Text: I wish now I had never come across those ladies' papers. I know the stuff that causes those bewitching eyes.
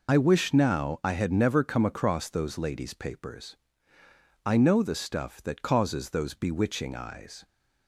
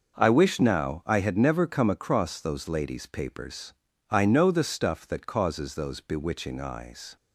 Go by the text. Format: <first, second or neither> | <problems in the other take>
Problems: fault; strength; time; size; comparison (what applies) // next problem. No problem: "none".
second | loses the start of "I"; at 0.0 s; 50 ms